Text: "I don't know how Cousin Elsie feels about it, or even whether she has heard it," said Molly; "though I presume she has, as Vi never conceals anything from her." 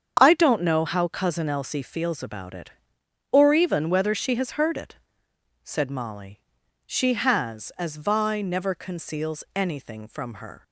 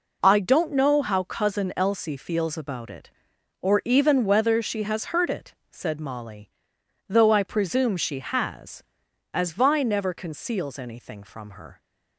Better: second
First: starts louder than the rest; strong; until 1.2 s; 7.5 dB // skips "though I presume"; at 6.6 s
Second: none

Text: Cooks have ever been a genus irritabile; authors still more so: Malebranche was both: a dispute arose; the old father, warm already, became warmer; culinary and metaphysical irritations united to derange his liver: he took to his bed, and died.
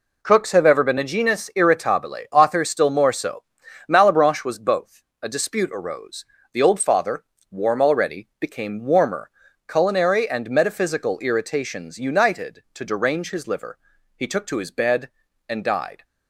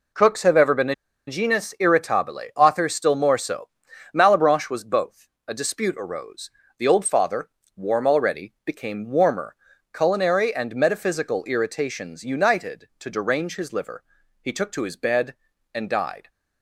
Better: first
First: none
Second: pauses between "a" and "genus"; slight; at 0.9 s; 0.32 s long

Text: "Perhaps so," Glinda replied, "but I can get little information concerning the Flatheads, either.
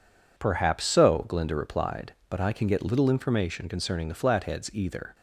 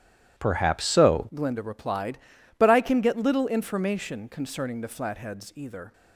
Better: first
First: none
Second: starts louder than the rest; strong; until 1.4 s; 12.5 dB // changes voice at "Glinda"; from 1.3 s on; 4.6 s long

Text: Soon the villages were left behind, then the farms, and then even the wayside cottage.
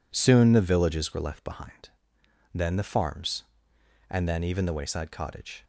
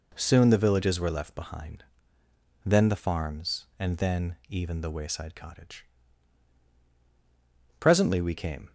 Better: first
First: none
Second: goes on to say "Presently we came"; noticeable; from 7.7 s on; 0.94 s long

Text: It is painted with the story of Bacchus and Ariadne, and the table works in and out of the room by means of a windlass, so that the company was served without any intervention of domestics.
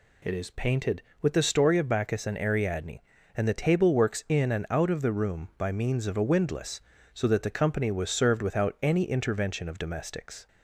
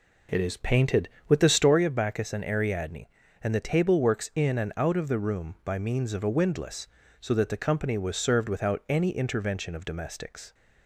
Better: first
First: none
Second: starts louder than the rest; until 1.8 s; 3.5 dB

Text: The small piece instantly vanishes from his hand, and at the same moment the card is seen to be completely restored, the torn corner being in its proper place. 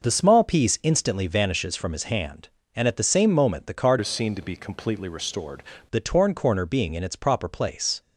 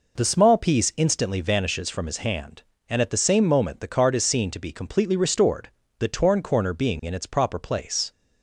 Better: second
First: changes voice from "is" to "restored"; from 4.0 to 5.6 s; 1.6 s long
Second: none

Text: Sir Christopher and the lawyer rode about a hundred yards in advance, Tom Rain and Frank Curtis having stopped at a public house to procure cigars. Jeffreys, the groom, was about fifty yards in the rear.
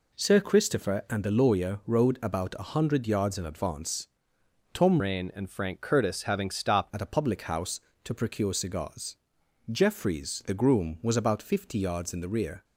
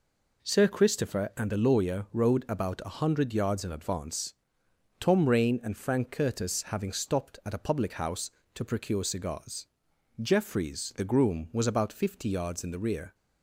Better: second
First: changes voice from "Rain" to "stopped"; from 5.0 to 6.8 s; 1.8 s long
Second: none

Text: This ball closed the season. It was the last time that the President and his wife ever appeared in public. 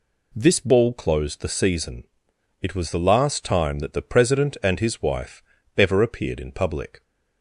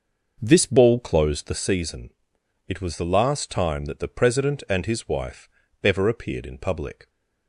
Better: first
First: pauses between "wife" and "ever"; slight; at 5.4 s; 0.34 s long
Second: starts louder than the rest; noticeable; until 1.7 s; 6 dB // pauses between "wife" and "ever"; slight; at 5.4 s; 0.34 s long

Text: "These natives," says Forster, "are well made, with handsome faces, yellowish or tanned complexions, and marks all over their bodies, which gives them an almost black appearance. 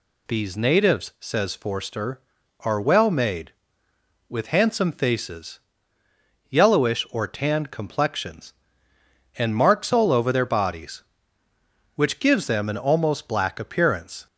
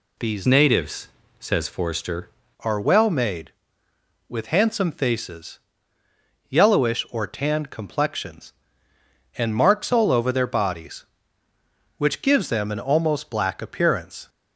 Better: first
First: none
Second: changes voice from "natives" to "Forster"; from 0.4 to 2.2 s; 1.8 s long

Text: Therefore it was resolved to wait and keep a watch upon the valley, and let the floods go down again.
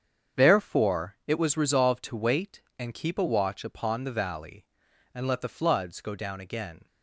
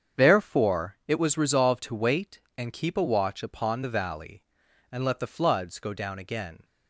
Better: neither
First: starts louder than the rest; strong; until 1.4 s; 7.5 dB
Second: starts louder than the rest; strong; until 1.3 s; 7.5 dB

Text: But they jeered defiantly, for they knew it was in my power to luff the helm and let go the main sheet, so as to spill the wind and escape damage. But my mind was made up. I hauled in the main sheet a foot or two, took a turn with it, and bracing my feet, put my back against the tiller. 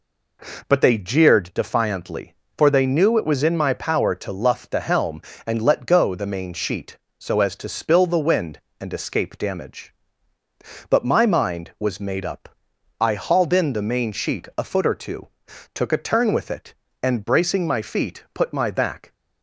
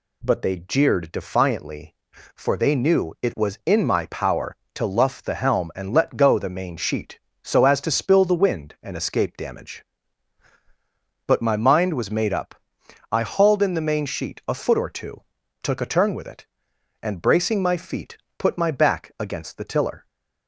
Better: second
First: stops before "against the tiller"; at 19.1 s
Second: none

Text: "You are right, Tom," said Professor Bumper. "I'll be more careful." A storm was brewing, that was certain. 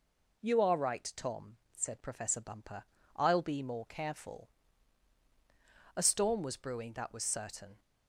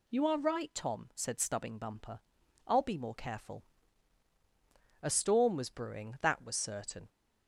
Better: first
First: none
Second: says "Stubbing" for "Professor"; at 1.4 s

